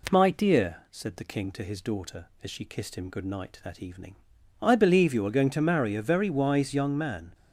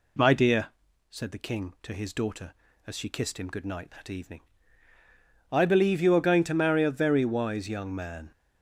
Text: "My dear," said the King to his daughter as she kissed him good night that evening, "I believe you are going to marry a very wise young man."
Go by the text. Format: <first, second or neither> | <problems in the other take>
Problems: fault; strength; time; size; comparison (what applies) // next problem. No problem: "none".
neither | none